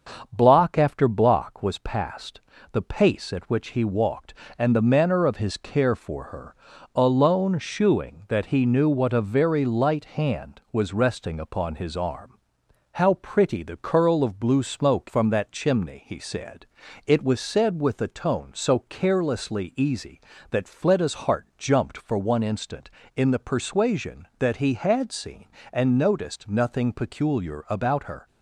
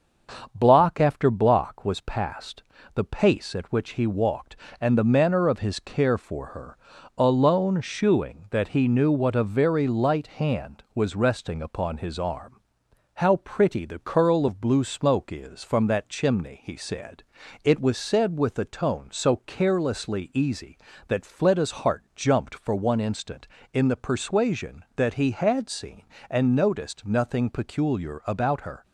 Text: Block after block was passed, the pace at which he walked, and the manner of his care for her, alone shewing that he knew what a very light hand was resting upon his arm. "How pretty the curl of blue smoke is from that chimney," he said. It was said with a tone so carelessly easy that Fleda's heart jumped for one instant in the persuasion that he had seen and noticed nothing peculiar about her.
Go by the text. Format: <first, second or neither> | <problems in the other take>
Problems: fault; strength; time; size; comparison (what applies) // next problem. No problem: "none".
second | starts louder than the rest; until 1.3 s; 7 dB; also in the second // skips "is"; at 15.0 s